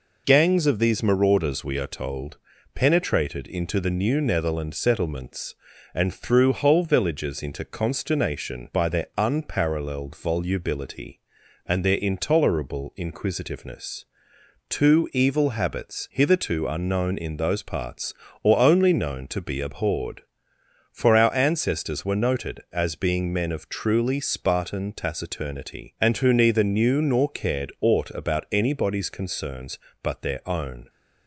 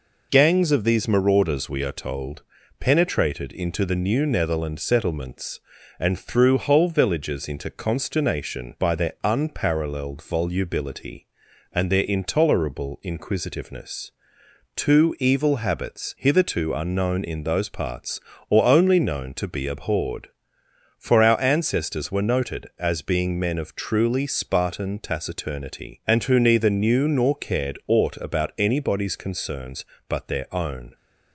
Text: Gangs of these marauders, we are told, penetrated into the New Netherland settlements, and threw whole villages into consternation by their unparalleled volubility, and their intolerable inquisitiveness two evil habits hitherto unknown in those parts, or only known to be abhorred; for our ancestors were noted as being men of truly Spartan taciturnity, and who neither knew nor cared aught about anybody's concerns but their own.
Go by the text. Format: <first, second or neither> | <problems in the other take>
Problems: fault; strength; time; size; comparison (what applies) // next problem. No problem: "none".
neither | pauses between "inquisitiveness" and "two"; noticeable; the same in both